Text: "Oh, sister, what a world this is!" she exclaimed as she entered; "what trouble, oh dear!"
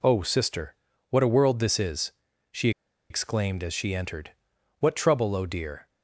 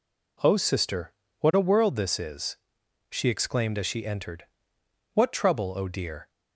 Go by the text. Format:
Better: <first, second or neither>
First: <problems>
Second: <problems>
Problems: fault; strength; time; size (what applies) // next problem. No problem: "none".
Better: second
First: pauses between "she" and "exclaimed"; at 2.6 s; 0.40 s long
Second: none